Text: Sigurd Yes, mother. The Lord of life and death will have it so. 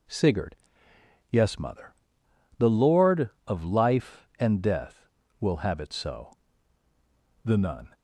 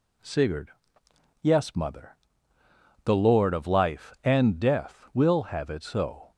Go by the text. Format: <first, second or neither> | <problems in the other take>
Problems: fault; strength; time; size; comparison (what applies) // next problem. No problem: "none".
second | pauses between "Sigurd" and "Yes"; noticeable; at 0.5 s; 0.74 s long; noticeable in the second // goes on to say "The Nun"; slight; from 7.4 s on; 0.46 s long